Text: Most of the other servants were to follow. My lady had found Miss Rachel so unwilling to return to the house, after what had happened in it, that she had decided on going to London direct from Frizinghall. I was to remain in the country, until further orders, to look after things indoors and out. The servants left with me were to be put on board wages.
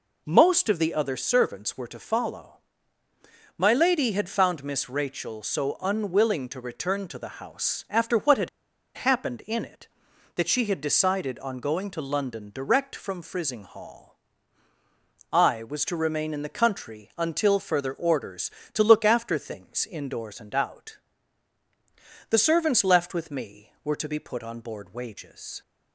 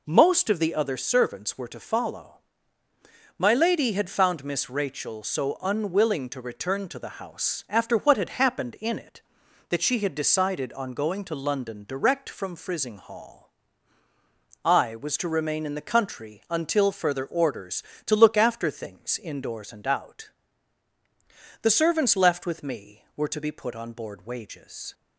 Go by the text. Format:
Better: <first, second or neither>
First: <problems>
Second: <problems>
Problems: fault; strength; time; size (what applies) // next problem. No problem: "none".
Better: second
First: pauses between "had" and "happened"; noticeable; at 8.4 s; 0.48 s long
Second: none